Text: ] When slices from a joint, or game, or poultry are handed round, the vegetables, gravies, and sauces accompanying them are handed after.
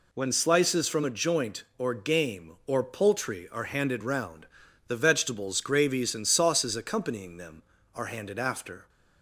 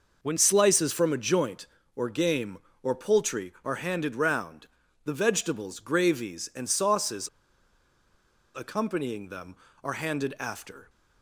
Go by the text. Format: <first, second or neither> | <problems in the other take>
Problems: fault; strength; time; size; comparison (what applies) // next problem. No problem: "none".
first | pauses between "sauces" and "accompanying"; strong; at 7.2 s; 1.2 s long